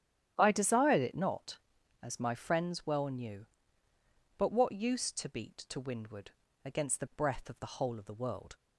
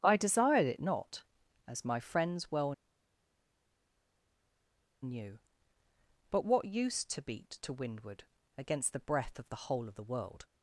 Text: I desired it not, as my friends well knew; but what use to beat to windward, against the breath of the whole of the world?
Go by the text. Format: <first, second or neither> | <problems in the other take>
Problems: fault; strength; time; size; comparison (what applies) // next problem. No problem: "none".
first | starts louder than the rest; strong; until 1.0 s; 10.5 dB; strong in the first // pauses between "well" and "knew"; strong; at 2.7 s; 2.3 s long